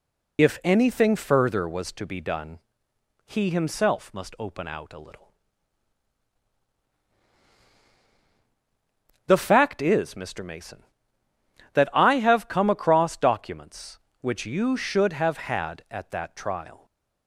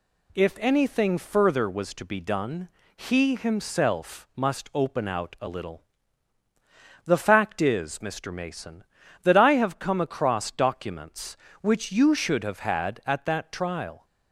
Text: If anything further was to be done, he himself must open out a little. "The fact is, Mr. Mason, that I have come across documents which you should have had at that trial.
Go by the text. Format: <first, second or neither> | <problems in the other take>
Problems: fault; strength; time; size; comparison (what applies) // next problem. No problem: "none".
second | loses the start of "If"; at 0.3 s; 35 ms